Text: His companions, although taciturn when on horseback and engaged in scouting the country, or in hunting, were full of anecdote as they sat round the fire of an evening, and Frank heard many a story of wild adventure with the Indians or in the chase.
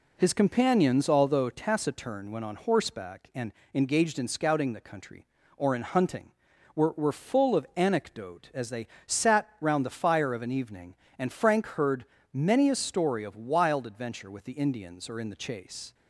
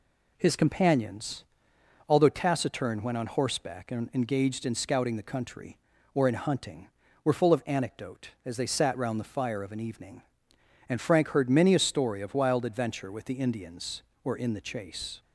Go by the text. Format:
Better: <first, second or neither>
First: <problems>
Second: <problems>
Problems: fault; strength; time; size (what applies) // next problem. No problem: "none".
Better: second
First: pauses between "and" and "engaged"; slight; at 3.5 s; 0.20 s long // says "were" twice; at 6.9 s // pauses between "they" and "sat"; slight; at 8.8 s; 0.18 s long // pauses between "heard" and "many"; slight; at 12.0 s; 0.30 s long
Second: none